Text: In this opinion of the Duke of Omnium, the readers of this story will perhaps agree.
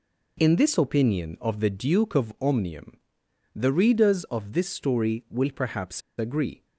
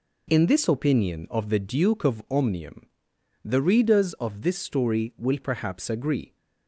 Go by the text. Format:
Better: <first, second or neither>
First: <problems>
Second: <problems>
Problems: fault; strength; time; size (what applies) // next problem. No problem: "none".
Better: second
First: pauses between "perhaps" and "agree"; slight; at 6.0 s; 0.17 s long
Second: none